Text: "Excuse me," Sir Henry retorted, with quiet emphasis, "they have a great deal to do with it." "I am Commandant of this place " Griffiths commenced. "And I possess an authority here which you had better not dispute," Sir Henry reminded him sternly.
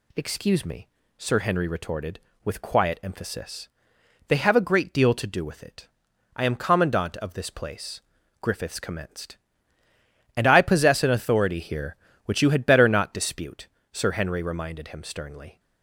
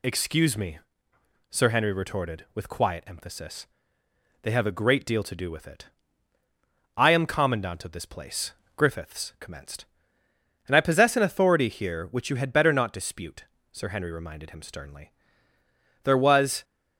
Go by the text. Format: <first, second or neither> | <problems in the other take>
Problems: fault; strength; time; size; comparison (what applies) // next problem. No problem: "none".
first | goes on to say "There was"; from 16.0 s on; 0.60 s long